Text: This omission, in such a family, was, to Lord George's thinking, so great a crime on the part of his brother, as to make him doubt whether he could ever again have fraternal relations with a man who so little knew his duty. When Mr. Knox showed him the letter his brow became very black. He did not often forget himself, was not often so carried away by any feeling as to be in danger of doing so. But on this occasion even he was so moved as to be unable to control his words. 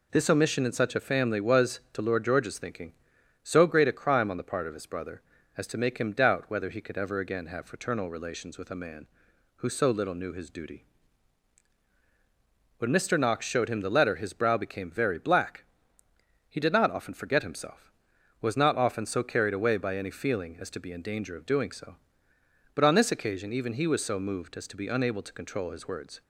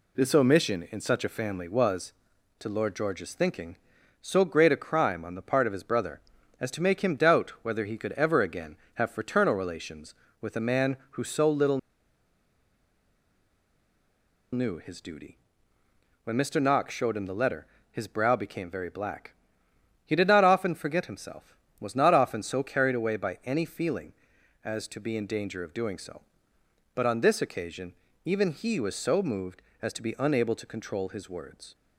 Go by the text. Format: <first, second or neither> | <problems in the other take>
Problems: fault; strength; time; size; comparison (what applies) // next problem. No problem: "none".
first | pauses between "little" and "knew"; strong; at 11.7 s; 2.7 s long // pauses between "letter" and "his"; slight; at 17.6 s; 0.24 s long // pauses between "occasion" and "even"; slight; at 27.9 s; 0.32 s long